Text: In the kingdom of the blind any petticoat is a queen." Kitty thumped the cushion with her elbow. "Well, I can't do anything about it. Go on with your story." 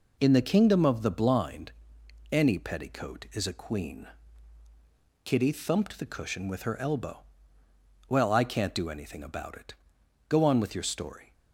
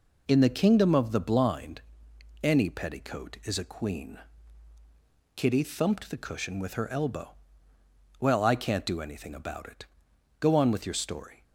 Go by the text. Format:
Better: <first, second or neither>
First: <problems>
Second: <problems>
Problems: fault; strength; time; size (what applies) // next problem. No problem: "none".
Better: neither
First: pauses between "blind" and "any"; noticeable; at 1.7 s; 0.58 s long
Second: pauses between "blind" and "any"; noticeable; at 1.8 s; 0.60 s long